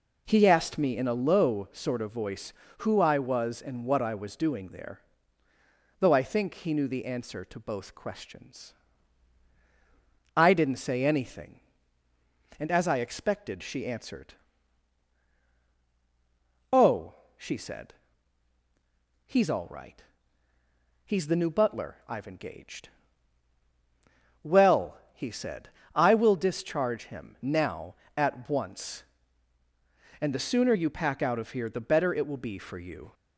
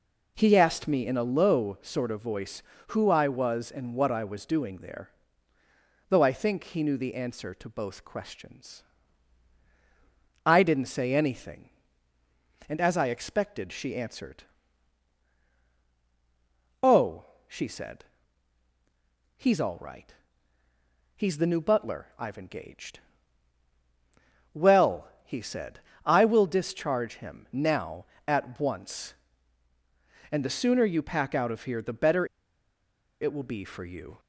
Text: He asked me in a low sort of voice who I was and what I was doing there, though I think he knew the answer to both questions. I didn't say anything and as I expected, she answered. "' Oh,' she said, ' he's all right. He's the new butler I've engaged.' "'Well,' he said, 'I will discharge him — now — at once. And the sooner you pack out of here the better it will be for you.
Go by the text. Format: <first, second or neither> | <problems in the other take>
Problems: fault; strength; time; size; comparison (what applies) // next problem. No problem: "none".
first | pauses between "better" and "it"; noticeable; at 32.2 s; 0.95 s long